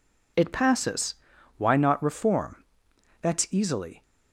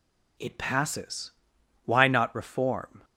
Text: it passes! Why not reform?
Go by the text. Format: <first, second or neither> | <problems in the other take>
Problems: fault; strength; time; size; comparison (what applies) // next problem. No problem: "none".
second | goes on to say "That's easily"; noticeable; from 3.2 s on; 0.82 s long